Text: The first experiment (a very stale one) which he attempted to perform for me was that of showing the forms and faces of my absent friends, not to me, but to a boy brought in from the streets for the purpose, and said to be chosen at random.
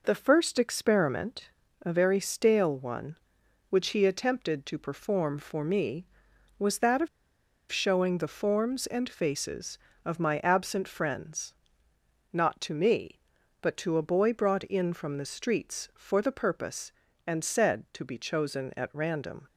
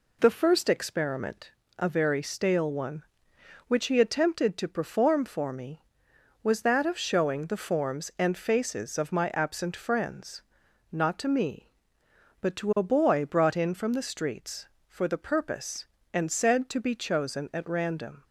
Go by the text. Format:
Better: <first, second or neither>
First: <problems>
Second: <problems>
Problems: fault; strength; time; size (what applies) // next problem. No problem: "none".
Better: second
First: pauses between "of" and "showing"; noticeable; at 7.0 s; 0.63 s long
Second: none